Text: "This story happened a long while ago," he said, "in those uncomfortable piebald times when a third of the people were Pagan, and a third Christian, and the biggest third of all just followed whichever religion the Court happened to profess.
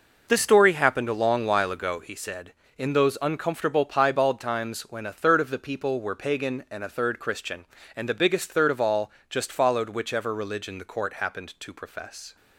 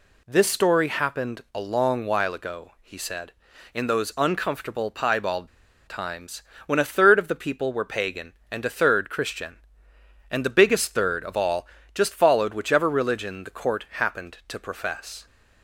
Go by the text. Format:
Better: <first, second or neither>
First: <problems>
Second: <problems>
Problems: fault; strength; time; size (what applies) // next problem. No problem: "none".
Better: first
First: pauses between "all" and "just"; slight; at 9.0 s; 0.20 s long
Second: pauses between "piebald" and "times"; at 5.4 s; 0.40 s long // pauses between "times" and "when"; slight; at 6.4 s; 0.24 s long // pauses between "all" and "just"; slight; at 11.6 s; 0.30 s long